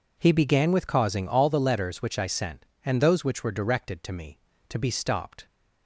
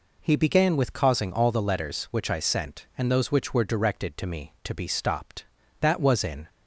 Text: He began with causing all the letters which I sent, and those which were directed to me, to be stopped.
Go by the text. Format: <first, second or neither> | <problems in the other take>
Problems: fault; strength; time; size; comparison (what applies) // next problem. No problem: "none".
first | goes on to say "That was in"; noticeable; from 5.8 s on; 0.68 s long